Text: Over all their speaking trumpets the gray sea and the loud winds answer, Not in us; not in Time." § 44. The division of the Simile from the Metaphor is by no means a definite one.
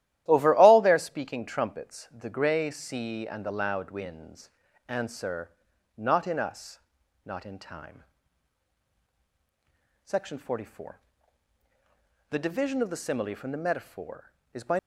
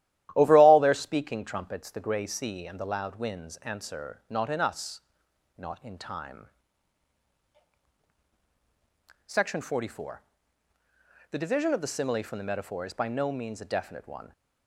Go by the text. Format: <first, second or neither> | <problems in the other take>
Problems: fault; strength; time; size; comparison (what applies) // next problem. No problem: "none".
second | starts louder than the rest; strong; until 1.2 s; 13.5 dB; strong in the second // pauses between "winds" and "answer"; at 4.4 s; 0.40 s long // stops before "no means a definite one"; at 14.7 s